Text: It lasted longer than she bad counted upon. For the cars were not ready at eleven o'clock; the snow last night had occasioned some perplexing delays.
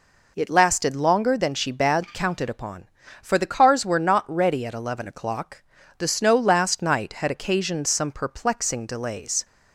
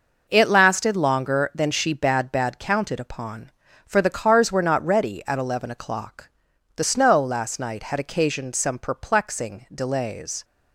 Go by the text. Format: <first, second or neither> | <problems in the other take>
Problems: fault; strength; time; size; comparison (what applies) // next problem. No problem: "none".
first | says "bad" twice; at 2.3 s